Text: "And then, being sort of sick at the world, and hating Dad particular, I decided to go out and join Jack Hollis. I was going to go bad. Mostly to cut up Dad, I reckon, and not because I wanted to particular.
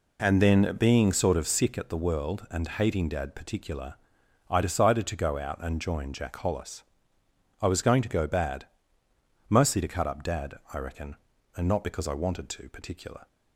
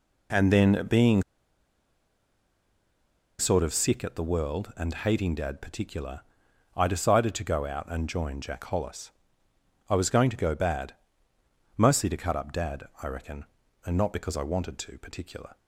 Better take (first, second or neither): first